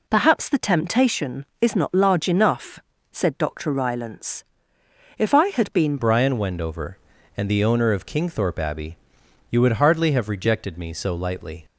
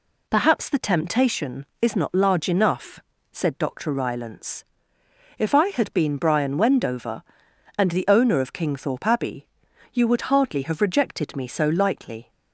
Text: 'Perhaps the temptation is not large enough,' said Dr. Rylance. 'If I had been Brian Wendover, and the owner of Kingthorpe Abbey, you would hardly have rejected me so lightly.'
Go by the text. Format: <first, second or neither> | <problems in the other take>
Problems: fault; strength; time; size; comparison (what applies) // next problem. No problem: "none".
second | changes voice at "Brian"; from 5.9 s on; 5.7 s long